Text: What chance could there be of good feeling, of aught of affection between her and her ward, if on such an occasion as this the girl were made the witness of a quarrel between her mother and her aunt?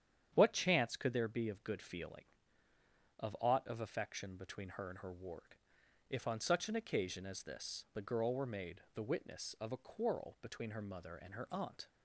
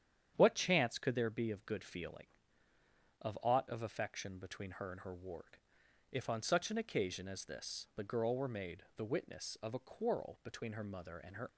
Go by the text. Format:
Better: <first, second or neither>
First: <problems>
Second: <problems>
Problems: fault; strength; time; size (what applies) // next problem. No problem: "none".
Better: first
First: starts louder than the rest; strong; until 1.3 s; 9 dB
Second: starts louder than the rest; strong; until 1.3 s; 9 dB // stops before "aunt"; at 11.4 s